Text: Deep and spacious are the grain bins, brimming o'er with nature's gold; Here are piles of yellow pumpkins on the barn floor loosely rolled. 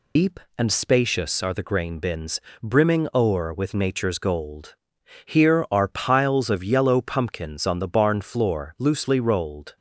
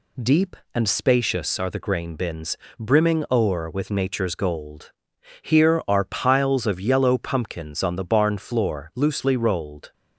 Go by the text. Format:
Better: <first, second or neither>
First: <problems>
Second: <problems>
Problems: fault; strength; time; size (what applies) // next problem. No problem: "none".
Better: second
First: loses the start of "Deep"; at 0.1 s; 145 ms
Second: none